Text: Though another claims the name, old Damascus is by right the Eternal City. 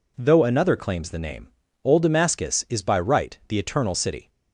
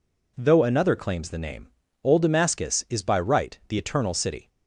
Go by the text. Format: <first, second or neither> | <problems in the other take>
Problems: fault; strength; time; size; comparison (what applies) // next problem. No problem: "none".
neither | none